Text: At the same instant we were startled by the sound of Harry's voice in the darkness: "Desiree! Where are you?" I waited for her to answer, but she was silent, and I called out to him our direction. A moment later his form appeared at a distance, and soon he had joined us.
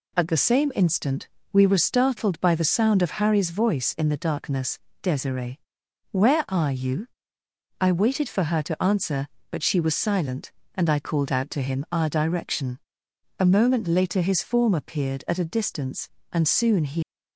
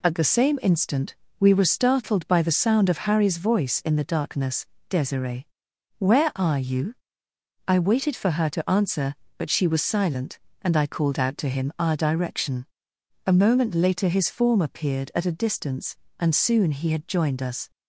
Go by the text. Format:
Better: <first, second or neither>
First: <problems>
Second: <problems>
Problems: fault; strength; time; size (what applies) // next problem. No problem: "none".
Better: second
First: pauses between "instant" and "we"; slight; at 1.2 s; 0.24 s long // stops before "had joined us"; at 17.0 s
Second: pauses between "instant" and "we"; slight; at 1.1 s; 0.24 s long